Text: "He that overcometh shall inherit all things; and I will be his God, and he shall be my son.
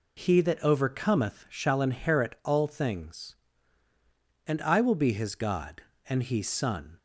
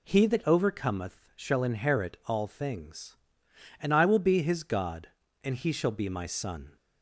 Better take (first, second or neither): second